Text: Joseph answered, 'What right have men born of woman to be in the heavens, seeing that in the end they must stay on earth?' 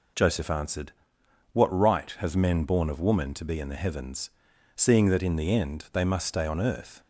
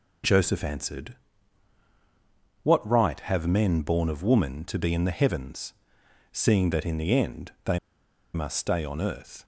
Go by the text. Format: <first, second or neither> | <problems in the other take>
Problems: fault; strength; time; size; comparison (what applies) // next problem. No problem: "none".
first | pauses between "they" and "must"; noticeable; at 7.7 s; 0.55 s long